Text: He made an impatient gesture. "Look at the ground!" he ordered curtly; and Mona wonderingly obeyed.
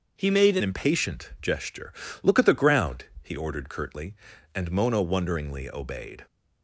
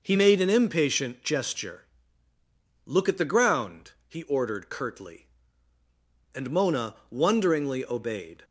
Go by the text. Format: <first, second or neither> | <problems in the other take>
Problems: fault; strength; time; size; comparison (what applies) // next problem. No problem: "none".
second | starts louder than the rest; noticeable; until 1.2 s; 6 dB // changes voice at "impatient"; from 0.6 s on; 5.6 s long